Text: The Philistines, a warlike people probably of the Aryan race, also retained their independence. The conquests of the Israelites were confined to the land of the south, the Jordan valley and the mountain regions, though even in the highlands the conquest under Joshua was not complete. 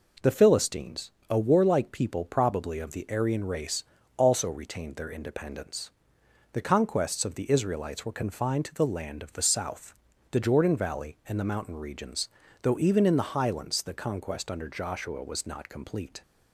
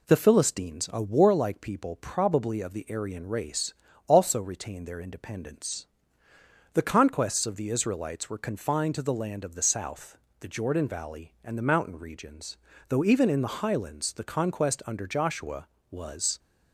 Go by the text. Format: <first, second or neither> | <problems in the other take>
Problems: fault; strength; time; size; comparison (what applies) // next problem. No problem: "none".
first | stops before "not complete"; at 16.3 s